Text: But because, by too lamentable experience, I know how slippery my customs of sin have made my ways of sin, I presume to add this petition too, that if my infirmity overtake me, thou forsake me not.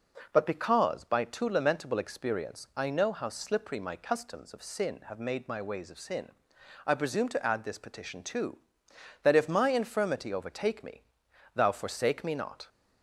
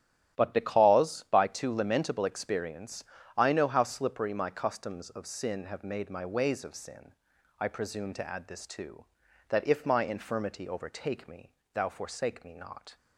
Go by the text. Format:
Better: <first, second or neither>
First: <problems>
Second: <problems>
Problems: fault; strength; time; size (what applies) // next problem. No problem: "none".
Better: first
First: none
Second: starts louder than the rest; strong; until 1.4 s; 11 dB // skips "petition"; at 8.6 s